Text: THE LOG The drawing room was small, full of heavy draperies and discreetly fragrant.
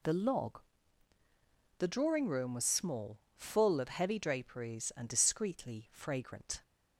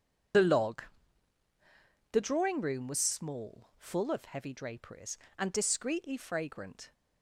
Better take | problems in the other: first | loses the start of "THE"; at 0.3 s; 35 ms // starts louder than the rest; strong; until 2.6 s; 7.5 dB // pauses between "LOG" and "The"; strong; at 0.8 s; 1.2 s long; also in the first

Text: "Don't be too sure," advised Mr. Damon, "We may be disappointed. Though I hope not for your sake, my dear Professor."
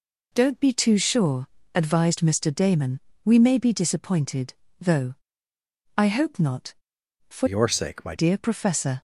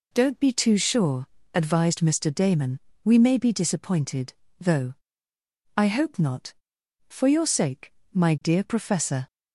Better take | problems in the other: second | pauses between "Though" and "I"; noticeable; at 5.1 s; 0.84 s long; noticeable in the second // changes voice from "your" to "my"; from 7.4 to 8.1 s; 0.7 s long

